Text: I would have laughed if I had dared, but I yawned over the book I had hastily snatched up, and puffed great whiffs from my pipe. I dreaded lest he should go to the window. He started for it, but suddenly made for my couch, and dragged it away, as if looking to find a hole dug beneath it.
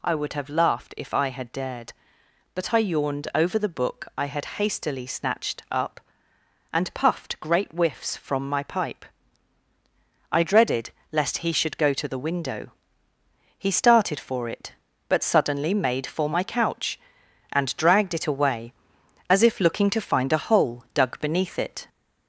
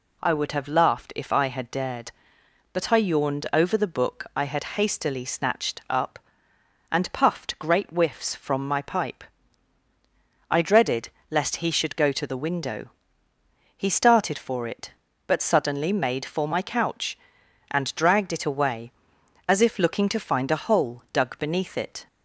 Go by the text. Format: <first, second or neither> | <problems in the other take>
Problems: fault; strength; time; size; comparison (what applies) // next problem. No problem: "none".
second | gets louder; slight; throughout; 3 dB // pauses between "dreaded" and "lest"; slight; at 10.9 s; 0.22 s long; slight in the second